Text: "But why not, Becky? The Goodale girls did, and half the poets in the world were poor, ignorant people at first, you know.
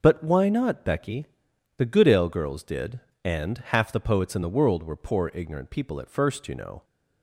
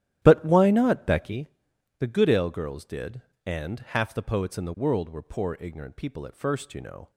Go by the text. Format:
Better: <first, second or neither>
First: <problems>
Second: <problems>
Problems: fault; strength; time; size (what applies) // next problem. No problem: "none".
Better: first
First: none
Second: starts louder than the rest; strong; until 1.5 s; 11.5 dB